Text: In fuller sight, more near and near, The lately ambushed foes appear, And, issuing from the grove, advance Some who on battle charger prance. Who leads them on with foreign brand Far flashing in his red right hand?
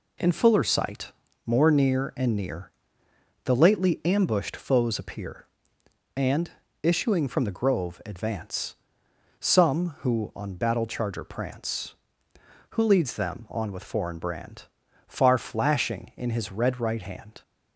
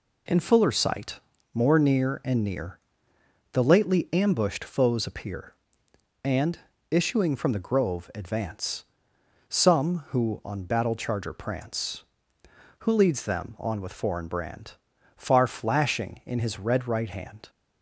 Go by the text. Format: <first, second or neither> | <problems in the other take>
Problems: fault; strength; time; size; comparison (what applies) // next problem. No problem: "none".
neither | pauses between "advance" and "Some"; noticeable; the same in both // pauses between "brand" and "Far"; the same in both